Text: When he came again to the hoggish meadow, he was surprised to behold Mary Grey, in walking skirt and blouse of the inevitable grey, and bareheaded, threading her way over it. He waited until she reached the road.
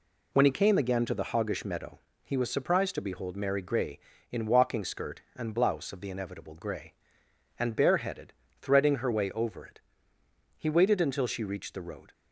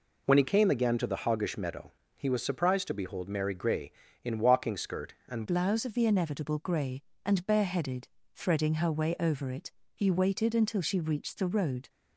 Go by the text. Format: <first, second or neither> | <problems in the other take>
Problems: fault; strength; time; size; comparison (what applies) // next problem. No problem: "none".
first | changes voice at "blouse"; from 5.4 s on; 6.4 s long